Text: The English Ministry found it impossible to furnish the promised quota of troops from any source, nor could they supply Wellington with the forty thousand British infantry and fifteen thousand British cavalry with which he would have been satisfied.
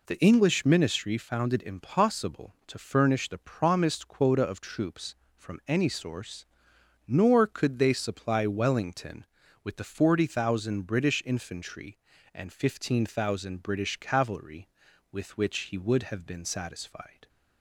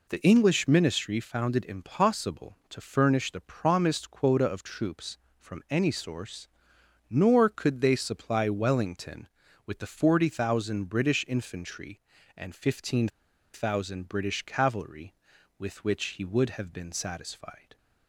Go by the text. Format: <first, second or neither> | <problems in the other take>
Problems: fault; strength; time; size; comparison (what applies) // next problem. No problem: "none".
first | pauses between "fifteen" and "thousand"; at 13.0 s; 0.44 s long